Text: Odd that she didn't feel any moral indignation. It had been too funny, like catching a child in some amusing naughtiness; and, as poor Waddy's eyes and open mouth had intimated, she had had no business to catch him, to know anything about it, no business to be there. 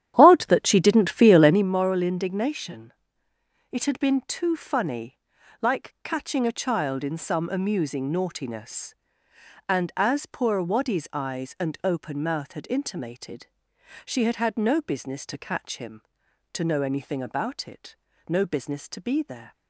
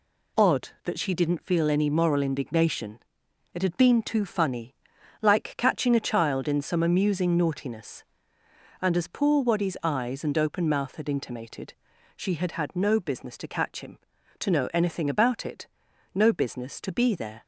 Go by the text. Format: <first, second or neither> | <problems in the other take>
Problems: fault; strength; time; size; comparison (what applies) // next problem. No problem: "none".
second | starts louder than the rest; strong; until 1.7 s; 10.5 dB